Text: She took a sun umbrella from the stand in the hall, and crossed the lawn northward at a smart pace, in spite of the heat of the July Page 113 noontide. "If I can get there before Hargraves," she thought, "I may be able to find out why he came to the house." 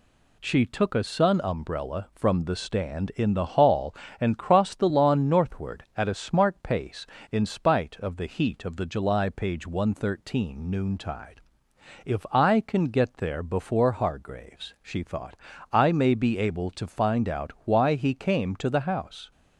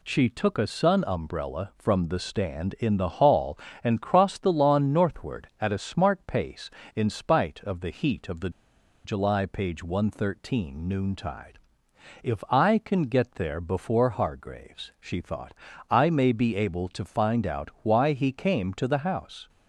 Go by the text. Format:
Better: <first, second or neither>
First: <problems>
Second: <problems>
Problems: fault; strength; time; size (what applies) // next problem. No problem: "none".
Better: first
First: none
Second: pauses between "the" and "July"; noticeable; at 8.4 s; 0.54 s long